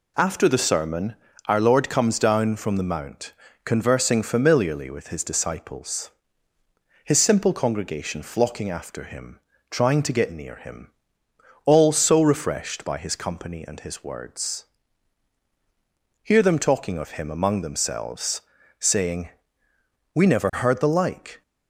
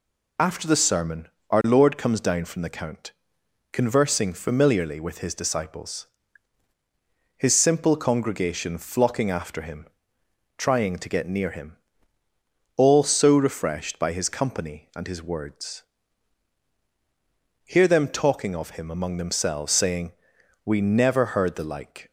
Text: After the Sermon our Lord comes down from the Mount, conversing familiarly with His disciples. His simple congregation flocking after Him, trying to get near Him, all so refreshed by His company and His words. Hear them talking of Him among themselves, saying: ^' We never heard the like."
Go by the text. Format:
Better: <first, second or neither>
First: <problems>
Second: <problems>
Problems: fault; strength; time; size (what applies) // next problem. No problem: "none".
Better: first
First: pauses between "Sermon" and "our"; slight; at 1.1 s; 0.32 s long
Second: pauses between "Sermon" and "our"; slight; at 1.2 s; 0.22 s long // says "Count" for "Mount"; at 2.6 s